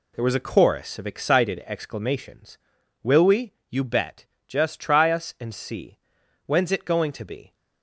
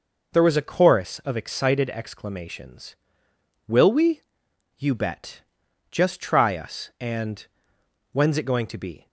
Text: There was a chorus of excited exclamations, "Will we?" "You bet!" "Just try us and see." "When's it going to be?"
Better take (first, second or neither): first